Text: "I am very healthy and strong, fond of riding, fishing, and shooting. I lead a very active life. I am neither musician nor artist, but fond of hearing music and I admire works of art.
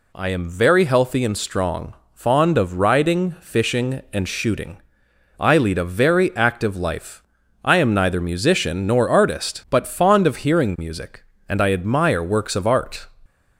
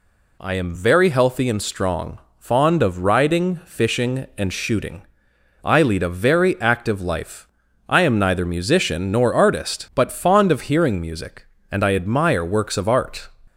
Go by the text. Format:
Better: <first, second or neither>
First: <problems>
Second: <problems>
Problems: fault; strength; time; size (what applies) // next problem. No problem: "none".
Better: neither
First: none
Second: none